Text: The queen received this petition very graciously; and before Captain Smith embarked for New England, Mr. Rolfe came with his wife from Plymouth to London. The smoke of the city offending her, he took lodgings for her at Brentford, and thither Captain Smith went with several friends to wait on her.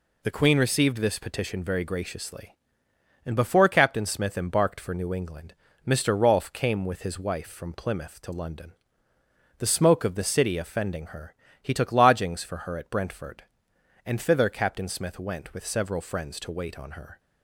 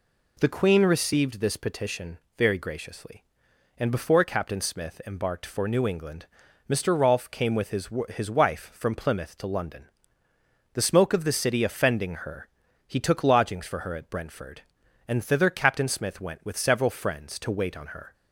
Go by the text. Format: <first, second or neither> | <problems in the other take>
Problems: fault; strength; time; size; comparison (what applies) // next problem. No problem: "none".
first | pauses between "petition" and "very"; slight; at 2.1 s; 0.20 s long // says "his" twice; at 8.0 s